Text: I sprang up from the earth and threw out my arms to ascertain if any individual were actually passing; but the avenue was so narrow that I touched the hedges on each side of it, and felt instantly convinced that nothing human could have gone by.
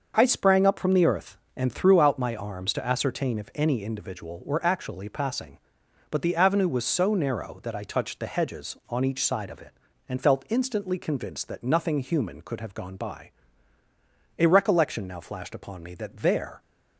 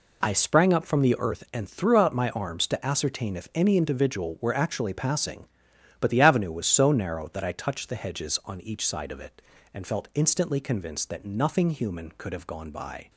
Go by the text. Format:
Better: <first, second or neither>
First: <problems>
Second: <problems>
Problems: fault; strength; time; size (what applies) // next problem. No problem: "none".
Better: second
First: starts louder than the rest; until 1.1 s; 6.5 dB // goes on to say "A recollection now flashed upon me that there"; strong; from 14.3 s on; 2.2 s long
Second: none